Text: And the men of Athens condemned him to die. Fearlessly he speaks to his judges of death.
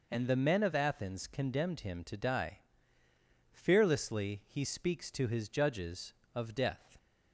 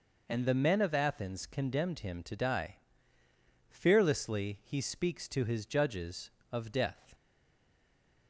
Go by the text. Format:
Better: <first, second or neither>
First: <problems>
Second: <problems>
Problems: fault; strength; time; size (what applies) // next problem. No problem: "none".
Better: first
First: none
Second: stays silent after the last word; from 7.1 s on; 1.1 s long